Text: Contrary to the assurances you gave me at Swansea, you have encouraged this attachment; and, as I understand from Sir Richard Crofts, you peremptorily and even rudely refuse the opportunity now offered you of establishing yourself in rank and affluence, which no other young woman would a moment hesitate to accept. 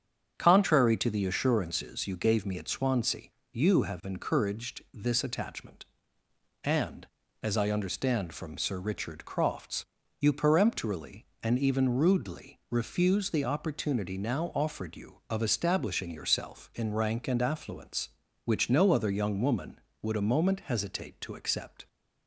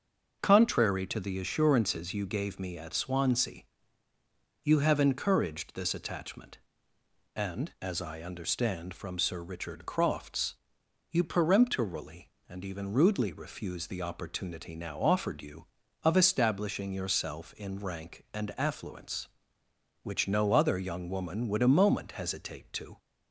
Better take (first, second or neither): first